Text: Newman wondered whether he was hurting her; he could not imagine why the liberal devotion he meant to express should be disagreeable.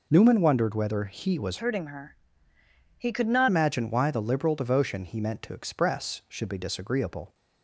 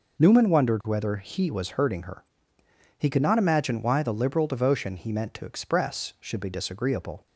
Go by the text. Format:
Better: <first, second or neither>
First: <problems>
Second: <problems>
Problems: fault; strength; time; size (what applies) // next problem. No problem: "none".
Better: second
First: changes voice from "hurting" to "not"; from 1.5 to 3.4 s; 1.9 s long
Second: none